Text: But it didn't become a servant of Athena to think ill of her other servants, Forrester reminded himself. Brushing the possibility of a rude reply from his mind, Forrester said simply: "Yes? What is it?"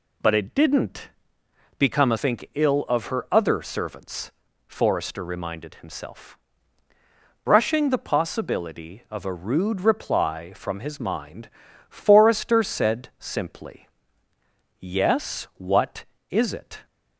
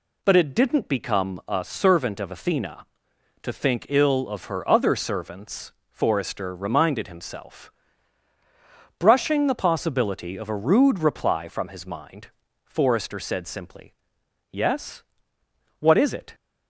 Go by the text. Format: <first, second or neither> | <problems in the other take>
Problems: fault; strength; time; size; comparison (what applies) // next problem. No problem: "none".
second | pauses between "didn't" and "become"; noticeable; at 1.0 s; 0.70 s long // skips "servant of Athena to"; at 2.1 s